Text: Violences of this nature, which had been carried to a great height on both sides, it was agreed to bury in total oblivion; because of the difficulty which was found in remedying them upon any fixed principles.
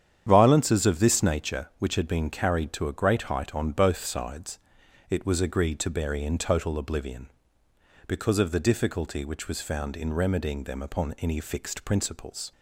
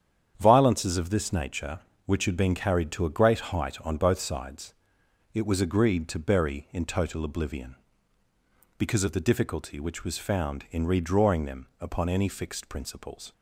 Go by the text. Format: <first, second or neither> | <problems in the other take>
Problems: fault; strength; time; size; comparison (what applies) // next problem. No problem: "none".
first | starts louder than the rest; strong; until 1.3 s; 8.5 dB; strong in the first // says "redrawing" for "remedying"; at 10.8 s